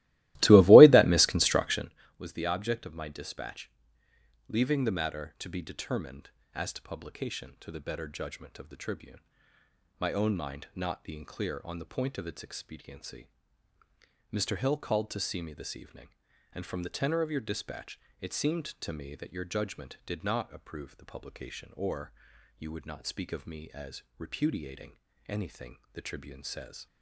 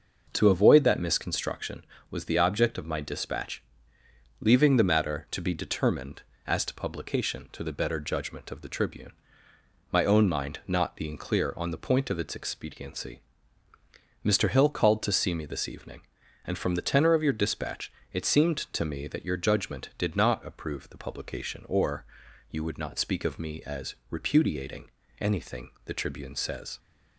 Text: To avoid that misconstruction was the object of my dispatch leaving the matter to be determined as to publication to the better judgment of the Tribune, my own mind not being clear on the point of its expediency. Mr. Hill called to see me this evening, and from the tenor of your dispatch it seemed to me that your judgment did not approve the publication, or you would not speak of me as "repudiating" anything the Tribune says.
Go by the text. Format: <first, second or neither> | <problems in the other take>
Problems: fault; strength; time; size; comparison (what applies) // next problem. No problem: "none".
second | starts louder than the rest; strong; until 2.0 s; 18 dB // pauses between "dispatch" and "leaving"; noticeable; at 3.7 s; 0.78 s long; noticeable in the second // pauses between "dispatch" and "it"; slight; at 17.9 s; 0.22 s long; slight in the second // pauses between "or" and "you"; at 22.1 s; 0.44 s long; also in the second // pauses between "repudiating" and "anything"; slight; at 24.9 s; 0.36 s long; slight in the second // pauses between "anything" and "the"; slight; at 25.7 s; 0.16 s long; slight in the second